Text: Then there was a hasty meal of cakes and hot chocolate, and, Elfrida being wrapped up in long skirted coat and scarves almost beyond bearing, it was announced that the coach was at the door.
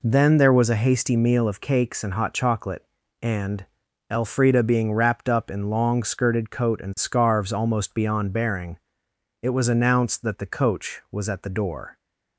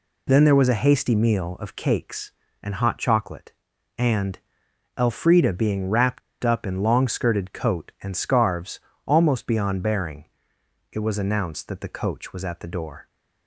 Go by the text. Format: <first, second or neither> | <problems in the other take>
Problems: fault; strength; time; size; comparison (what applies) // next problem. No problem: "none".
first | pauses between "wrapped" and "up"; slight; at 6.2 s; 0.22 s long // pauses between "scarves" and "almost"; slight; at 8.8 s; 0.26 s long